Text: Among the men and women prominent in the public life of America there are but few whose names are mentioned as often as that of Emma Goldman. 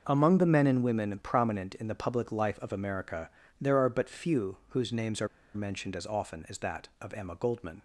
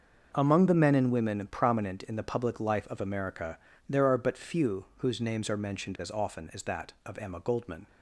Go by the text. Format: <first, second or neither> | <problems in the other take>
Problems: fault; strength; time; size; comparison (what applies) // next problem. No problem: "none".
second | starts louder than the rest; noticeable; until 1.0 s; 6 dB; noticeable in the second // pauses between "America" and "there"; slight; at 3.2 s; 0.28 s long; slight in the second // pauses between "are" and "mentioned"; slight; at 5.2 s; 0.28 s long